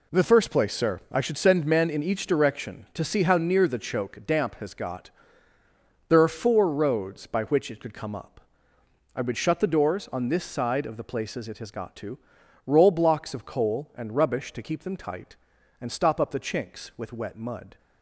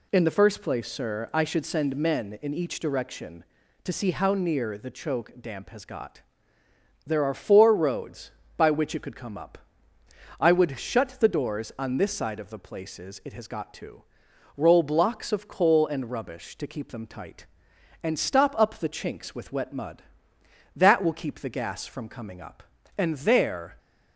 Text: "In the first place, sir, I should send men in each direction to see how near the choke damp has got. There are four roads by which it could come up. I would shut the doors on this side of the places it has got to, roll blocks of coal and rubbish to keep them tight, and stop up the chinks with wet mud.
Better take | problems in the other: first | goes on to say "That will keep the gas from coming up and there"; strong; from 20.7 s on; 3.0 s long

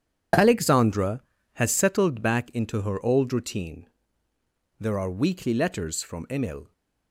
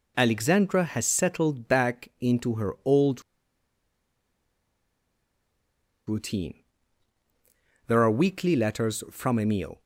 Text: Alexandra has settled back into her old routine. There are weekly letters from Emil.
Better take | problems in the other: first | pauses between "old" and "routine"; strong; at 3.2 s; 2.8 s long

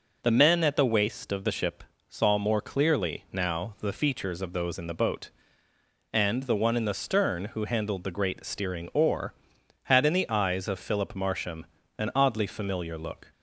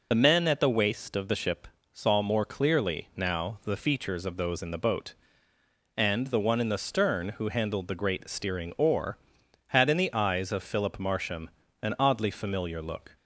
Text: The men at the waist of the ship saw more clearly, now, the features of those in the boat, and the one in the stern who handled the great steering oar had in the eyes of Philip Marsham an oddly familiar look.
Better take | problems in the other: first | loses the start of "The"; at 0.1 s; 35 ms // pauses between "ship" and "saw"; slight; at 1.6 s; 0.26 s long; slight in the first // pauses between "Marsham" and "an"; slight; at 11.4 s; 0.32 s long; slight in the first

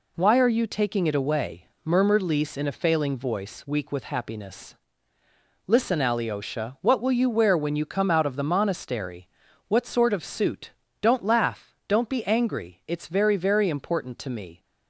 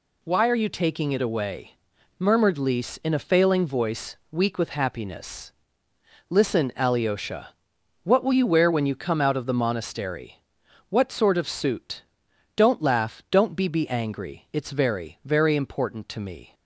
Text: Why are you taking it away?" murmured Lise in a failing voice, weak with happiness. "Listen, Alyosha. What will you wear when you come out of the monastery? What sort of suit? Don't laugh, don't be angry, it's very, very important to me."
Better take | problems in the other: first | says "be" twice; at 13.6 s

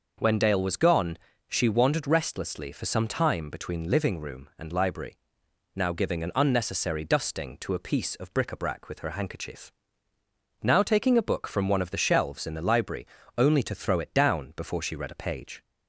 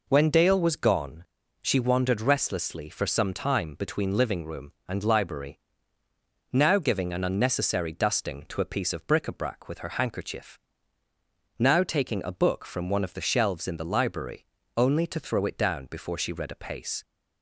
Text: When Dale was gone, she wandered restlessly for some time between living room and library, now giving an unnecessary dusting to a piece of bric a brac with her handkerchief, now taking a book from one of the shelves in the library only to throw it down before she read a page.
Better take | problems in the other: first | pauses between "library" and "only"; slight; at 14.4 s; 0.32 s long; slight in the first // says "pace" for "page"; at 16.5 s

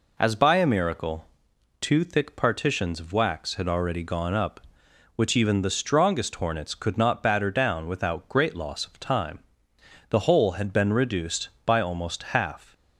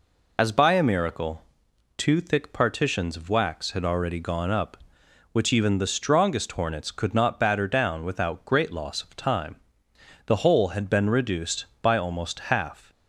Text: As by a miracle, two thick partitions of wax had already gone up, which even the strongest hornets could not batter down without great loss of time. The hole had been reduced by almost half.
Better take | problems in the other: first | loses the start of "As"; at 0.3 s; 30 ms

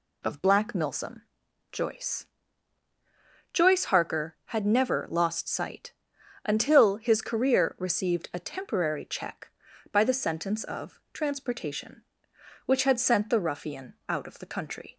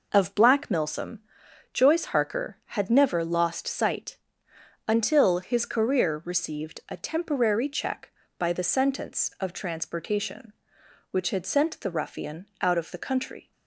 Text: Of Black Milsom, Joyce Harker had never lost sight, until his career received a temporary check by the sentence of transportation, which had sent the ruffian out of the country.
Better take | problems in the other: second | says "Joyce" twice; at 3.5 s

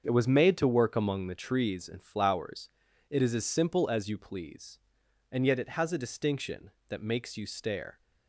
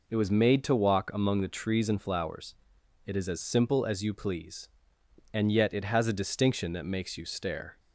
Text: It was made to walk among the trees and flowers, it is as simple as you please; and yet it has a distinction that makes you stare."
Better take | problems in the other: second | starts louder than the rest; until 1.0 s; 7 dB // says "work" for "walk"; at 0.6 s

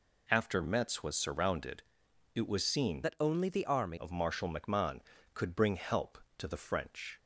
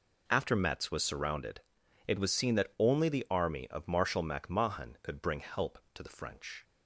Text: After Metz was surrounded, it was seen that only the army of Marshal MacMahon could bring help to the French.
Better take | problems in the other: second | changes voice from "that" to "army"; from 3.0 to 3.9 s; 0.9 s long

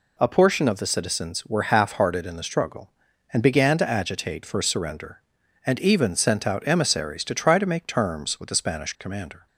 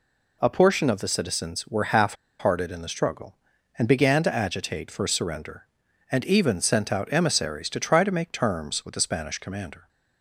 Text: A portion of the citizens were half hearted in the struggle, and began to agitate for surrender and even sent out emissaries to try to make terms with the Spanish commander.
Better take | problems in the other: first | pauses between "half" and "hearted"; slight; at 2.1 s; 0.25 s long

